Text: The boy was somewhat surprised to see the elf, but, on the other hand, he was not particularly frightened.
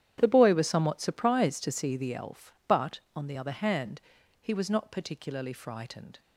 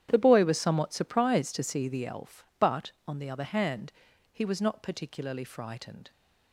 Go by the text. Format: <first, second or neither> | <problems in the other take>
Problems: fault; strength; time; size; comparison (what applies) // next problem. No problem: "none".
neither | starts louder than the rest; strong; the same in both